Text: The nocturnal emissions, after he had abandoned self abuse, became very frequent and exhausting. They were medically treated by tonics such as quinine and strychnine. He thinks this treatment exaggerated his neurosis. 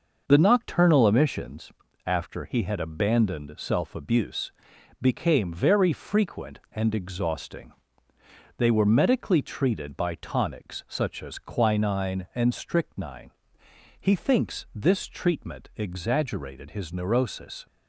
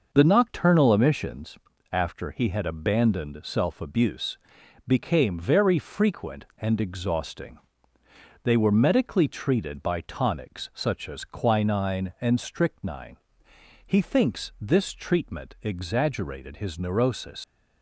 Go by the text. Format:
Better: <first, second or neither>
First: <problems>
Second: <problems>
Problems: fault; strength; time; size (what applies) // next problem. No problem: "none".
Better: first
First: none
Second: leaves "neurosis" unfinished; at 17.4 s; 75 ms